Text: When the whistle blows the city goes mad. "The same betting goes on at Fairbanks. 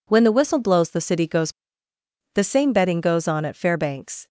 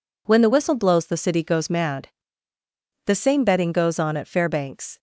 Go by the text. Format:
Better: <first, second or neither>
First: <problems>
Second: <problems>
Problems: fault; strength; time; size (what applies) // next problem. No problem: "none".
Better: second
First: skips "mad"; at 1.9 s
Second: none